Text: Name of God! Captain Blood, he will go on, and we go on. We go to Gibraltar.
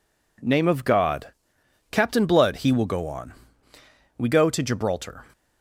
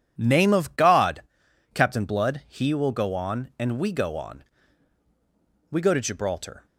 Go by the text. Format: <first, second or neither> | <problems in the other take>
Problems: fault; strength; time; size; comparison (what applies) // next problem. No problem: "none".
second | skips "and we go on"; at 3.7 s